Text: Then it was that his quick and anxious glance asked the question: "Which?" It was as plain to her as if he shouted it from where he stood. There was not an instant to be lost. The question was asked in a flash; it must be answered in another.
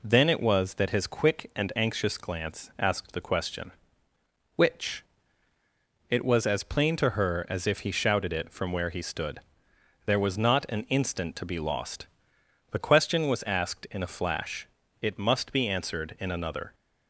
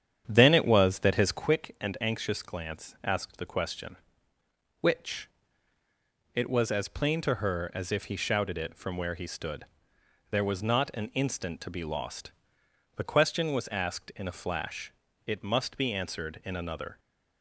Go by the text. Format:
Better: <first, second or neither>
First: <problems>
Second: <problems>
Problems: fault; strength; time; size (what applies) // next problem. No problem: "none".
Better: first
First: none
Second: starts louder than the rest; strong; until 1.5 s; 9 dB